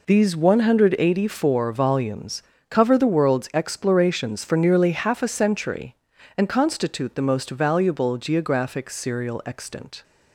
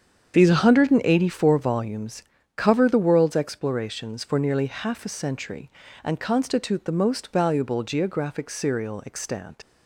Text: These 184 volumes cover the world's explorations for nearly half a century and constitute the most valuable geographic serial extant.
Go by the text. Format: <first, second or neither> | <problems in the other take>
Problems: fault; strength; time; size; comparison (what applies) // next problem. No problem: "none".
first | starts louder than the rest; strong; until 1.4 s; 8 dB // pauses between "volumes" and "cover"; slight; at 2.2 s; 0.36 s long; slight in the first // leaves "extant" unfinished; at 9.6 s; 90 ms